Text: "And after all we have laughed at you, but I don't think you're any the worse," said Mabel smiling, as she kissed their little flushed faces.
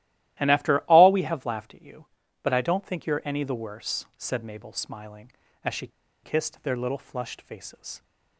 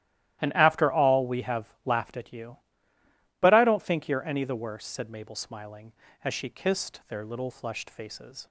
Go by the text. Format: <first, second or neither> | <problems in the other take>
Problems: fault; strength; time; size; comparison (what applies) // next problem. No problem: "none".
second | starts louder than the rest; strong; until 1.4 s; 14.5 dB; strong in the second // pauses between "she" and "kissed"; slight; at 5.8 s; 0.35 s long